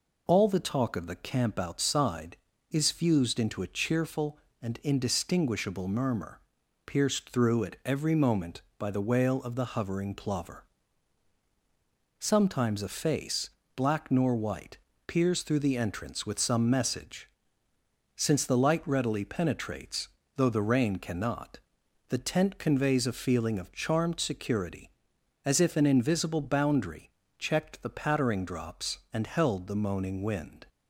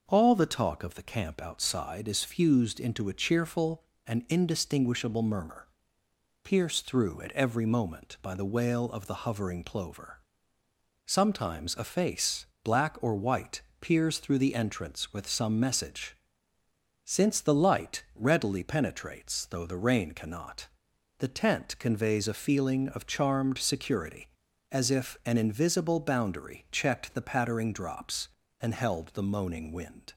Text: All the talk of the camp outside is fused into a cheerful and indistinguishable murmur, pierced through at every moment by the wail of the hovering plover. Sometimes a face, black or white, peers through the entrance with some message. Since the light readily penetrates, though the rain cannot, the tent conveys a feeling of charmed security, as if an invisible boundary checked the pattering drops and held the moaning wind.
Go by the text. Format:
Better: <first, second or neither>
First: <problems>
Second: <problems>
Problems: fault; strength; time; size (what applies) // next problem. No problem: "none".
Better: second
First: says "nor" for "or"; at 14.1 s // pauses between "boundary" and "checked"; slight; at 27.1 s; 0.28 s long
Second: none